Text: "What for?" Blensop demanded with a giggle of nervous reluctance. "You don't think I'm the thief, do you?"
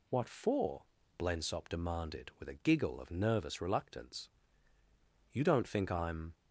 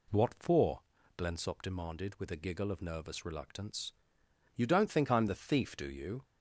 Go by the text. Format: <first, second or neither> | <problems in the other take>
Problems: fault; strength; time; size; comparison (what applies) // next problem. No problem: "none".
second | stops before "the thief do you"; at 6.3 s